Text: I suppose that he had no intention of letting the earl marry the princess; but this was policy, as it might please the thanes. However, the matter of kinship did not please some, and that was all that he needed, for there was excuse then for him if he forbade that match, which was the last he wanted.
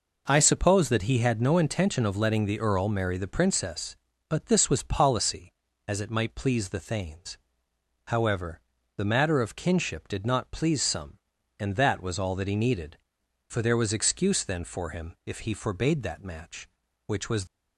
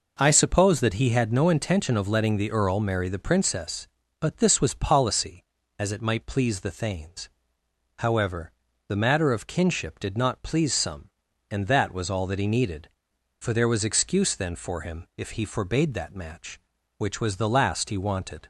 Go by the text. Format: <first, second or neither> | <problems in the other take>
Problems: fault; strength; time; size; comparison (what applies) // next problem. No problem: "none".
second | stops before "the last he wanted"; at 17.4 s